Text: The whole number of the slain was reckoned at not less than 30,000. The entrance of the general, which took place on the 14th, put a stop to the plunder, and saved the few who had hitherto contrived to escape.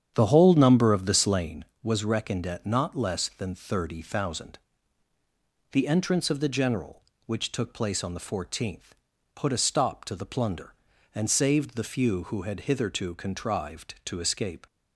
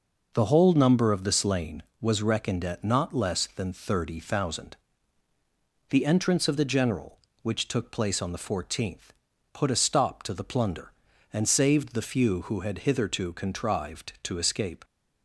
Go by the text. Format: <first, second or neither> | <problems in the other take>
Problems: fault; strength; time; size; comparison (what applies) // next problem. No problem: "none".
second | starts louder than the rest; strong; until 1.6 s; 9 dB